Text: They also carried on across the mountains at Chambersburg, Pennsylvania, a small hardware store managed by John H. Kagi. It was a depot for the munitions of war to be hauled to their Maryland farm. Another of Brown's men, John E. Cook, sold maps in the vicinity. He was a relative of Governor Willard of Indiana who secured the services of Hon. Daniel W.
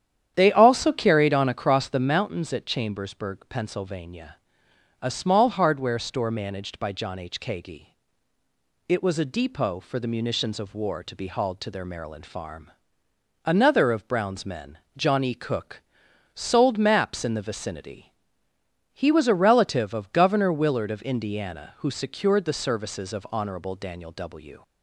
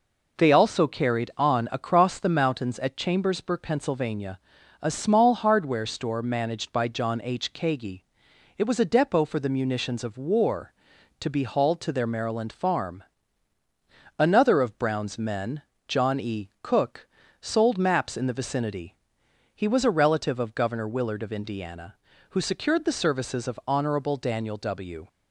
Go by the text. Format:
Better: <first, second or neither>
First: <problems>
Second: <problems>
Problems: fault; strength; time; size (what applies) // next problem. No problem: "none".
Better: second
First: starts louder than the rest; strong; until 2.2 s; 9.5 dB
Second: none